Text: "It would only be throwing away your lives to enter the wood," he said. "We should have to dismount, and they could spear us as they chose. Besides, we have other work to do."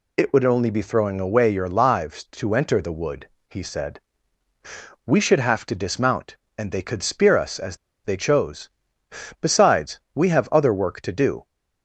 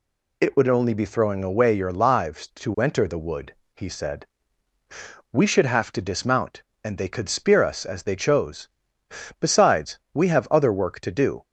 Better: second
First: pauses between "as" and "they"; slight; at 7.7 s; 0.27 s long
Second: none

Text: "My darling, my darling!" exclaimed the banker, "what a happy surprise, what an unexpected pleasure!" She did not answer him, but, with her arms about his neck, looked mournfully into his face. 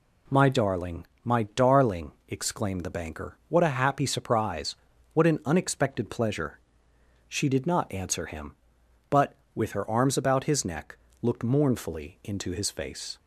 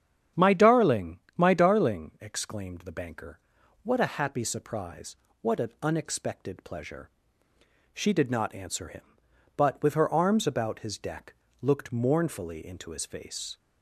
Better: first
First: none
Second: starts louder than the rest; strong; until 1.5 s; 8.5 dB // says "deck" for "neck"; at 10.9 s

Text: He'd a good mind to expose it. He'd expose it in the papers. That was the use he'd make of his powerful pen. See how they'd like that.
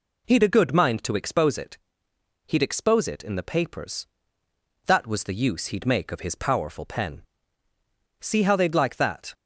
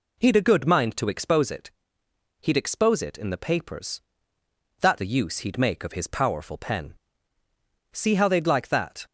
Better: first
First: none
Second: skips "was"; at 4.9 s

